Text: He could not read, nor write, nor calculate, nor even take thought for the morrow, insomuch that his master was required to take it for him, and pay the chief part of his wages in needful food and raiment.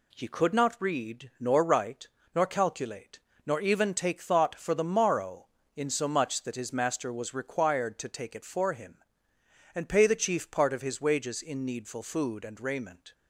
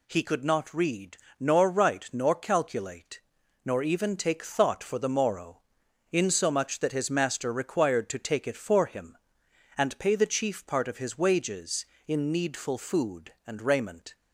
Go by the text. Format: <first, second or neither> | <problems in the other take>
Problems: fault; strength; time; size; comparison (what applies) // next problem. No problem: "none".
first | skips "was"; at 7.5 s